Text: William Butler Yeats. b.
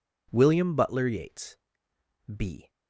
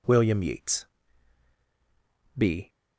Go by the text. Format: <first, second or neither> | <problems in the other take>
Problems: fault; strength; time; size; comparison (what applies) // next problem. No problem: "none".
first | skips "Butler"; at 0.4 s